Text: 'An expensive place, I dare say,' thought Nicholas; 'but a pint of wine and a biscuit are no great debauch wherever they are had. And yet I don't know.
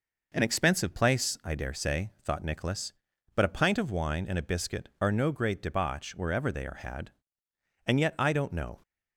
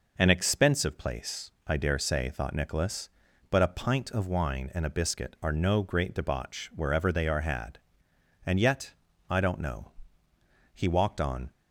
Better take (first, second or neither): first